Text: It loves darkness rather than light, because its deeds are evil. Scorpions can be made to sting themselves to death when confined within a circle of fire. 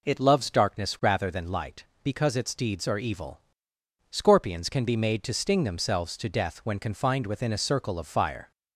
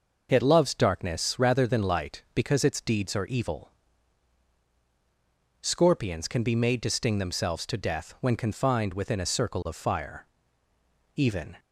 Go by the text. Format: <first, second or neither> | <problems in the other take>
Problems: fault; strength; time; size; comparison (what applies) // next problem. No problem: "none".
first | goes on to say "Even"; slight; from 11.1 s on; 0.42 s long